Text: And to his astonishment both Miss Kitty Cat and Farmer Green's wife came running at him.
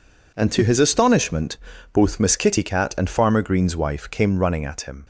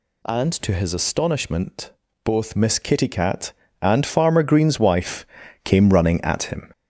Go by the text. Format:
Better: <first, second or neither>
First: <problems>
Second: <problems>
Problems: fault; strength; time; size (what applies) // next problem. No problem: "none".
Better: first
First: pauses between "astonishment" and "both"; slight; at 1.5 s; 0.36 s long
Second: gets louder; noticeable; throughout; 4.5 dB // pauses between "astonishment" and "both"; slight; at 1.9 s; 0.30 s long // pauses between "wife" and "came"; at 5.2 s; 0.38 s long